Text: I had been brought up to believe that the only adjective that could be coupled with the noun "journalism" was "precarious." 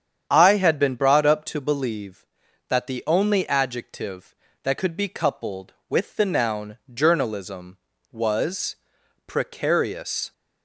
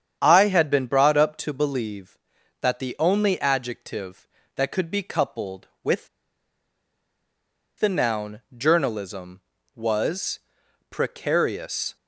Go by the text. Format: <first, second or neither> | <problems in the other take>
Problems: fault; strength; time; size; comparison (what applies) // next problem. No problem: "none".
first | starts louder than the rest; strong; until 1.2 s; 8.5 dB; strong in the first // pauses between "with" and "the"; strong; at 6.0 s; 1.7 s long // pauses between "noun" and "journalism"; slight; at 8.3 s; 0.16 s long; slight in the first // pauses between "was" and "precarious"; noticeable; at 10.3 s; 0.50 s long; noticeable in the first